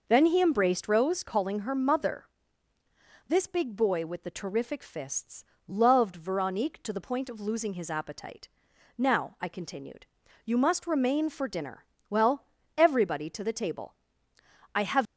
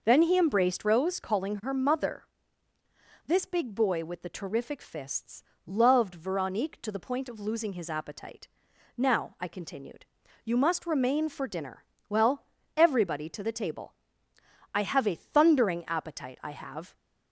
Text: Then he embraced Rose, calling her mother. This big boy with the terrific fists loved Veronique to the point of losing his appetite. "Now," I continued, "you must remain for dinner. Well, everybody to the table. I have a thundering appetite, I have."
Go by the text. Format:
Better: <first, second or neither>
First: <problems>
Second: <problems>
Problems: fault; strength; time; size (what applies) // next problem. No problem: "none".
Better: second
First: pauses between "fists" and "loved"; slight; at 5.4 s; 0.22 s long // stops before "a thundering appetite I have"; at 15.0 s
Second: pauses between "fists" and "loved"; slight; at 5.4 s; 0.22 s long